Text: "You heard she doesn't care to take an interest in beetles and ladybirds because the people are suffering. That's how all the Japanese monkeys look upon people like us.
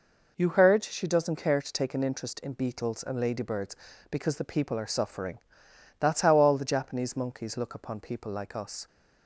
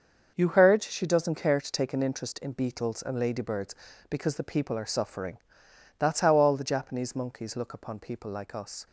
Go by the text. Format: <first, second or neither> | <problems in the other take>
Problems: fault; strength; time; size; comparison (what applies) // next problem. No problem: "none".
first | gets quieter; strong; throughout; 9 dB